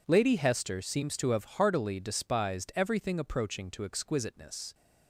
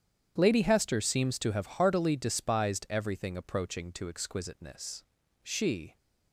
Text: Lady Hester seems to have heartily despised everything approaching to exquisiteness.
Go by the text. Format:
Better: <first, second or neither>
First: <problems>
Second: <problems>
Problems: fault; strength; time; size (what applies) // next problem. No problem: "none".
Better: first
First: none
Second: starts louder than the rest; strong; until 1.3 s; 9 dB // goes on to say "She"; from 5.4 s on; 0.54 s long